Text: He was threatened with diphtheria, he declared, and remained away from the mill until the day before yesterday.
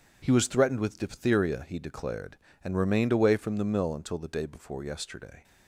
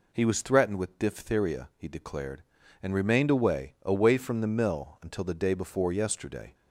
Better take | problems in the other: first | says "away" twice; at 3.8 s

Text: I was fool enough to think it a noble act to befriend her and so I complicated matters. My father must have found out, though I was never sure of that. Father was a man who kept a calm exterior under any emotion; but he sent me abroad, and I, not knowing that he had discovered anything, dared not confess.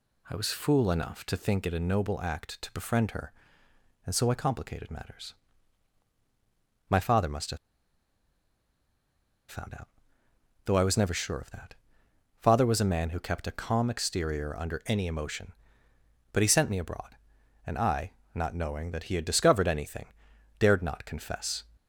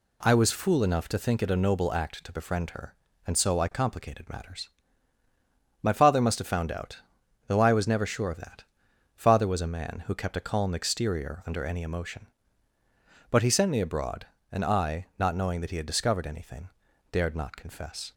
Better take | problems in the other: second | pauses between "have" and "found"; strong; at 7.5 s; 1.9 s long

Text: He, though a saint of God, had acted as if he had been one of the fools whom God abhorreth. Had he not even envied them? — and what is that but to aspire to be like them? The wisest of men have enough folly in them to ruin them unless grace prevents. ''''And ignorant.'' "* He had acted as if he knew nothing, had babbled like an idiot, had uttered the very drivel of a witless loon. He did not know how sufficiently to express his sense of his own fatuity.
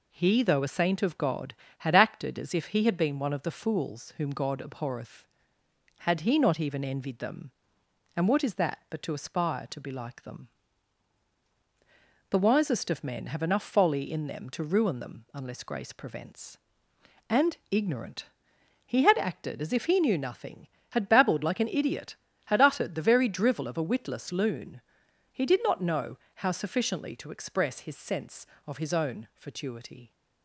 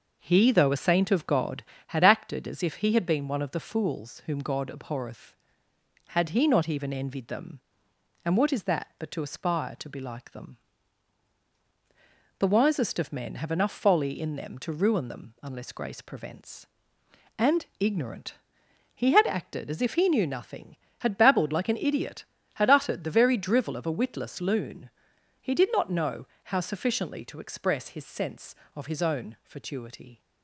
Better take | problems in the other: first | starts louder than the rest; noticeable; until 1.9 s; 6 dB // pauses between "And" and "ignorant"; slight; at 17.6 s; 0.16 s long; slight in the first // pauses between "know" and "how"; slight; at 26.2 s; 0.26 s long; slight in the first

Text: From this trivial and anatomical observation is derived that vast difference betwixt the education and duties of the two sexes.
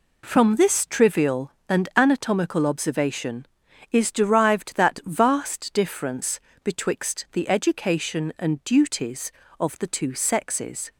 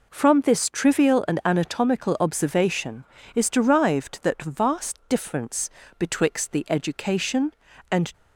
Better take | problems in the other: first | pauses between "difference" and "betwixt"; slight; at 5.6 s; 0.30 s long; slight in the first // stops before "duties of the two sexes"; at 8.1 s

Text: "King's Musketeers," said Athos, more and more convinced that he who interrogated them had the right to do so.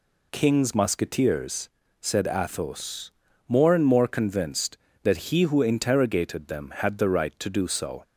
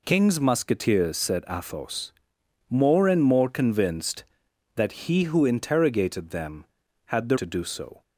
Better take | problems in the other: first | skips "right"; at 7.3 s

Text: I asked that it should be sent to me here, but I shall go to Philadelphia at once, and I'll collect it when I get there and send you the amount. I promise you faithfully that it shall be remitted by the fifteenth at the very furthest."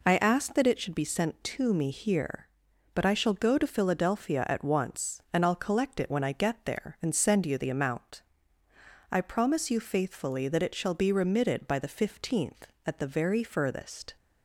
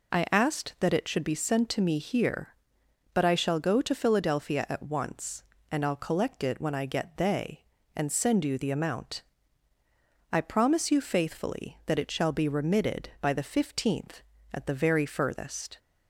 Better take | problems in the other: first | says "they" for "there"; at 7.1 s

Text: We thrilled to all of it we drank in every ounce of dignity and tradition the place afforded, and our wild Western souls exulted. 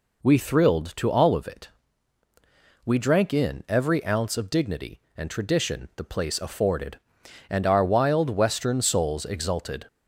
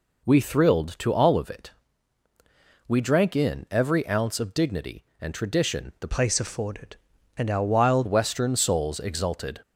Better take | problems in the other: first | pauses between "it" and "we"; at 1.7 s; 1.1 s long; also in the first // changes voice from "place" to "wild"; from 6.0 to 8.0 s; 2.0 s long

